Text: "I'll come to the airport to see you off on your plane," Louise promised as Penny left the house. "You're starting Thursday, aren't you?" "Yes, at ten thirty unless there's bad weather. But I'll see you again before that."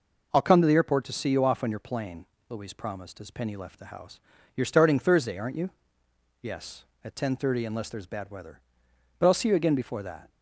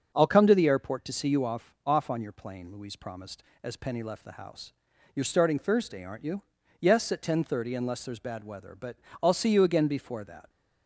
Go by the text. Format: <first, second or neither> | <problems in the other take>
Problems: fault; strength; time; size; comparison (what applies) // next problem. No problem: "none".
first | starts louder than the rest; until 1.1 s; 7 dB // says "off" twice; at 1.8 s // pauses between "But" and "I'll"; slight; at 8.9 s; 0.28 s long